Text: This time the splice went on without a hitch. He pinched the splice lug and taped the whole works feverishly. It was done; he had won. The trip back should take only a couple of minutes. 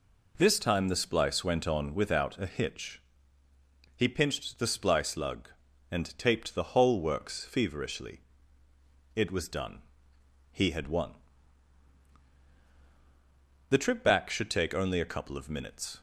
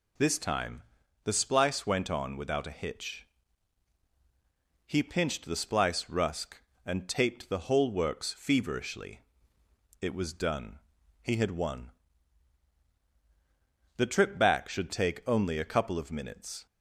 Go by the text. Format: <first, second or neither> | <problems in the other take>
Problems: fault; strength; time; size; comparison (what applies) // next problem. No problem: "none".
first | pauses between "time" and "the"; at 0.8 s; 0.40 s long // says "rusk" for "lug"; at 6.0 s